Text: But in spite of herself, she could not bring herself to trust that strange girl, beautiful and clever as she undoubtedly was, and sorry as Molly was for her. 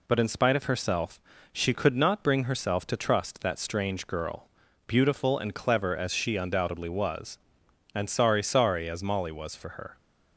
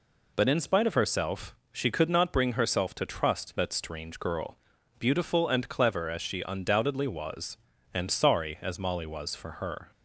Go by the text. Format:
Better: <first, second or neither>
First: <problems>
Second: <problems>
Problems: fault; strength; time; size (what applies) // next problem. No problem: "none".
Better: second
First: says "sorry" twice; at 8.4 s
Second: none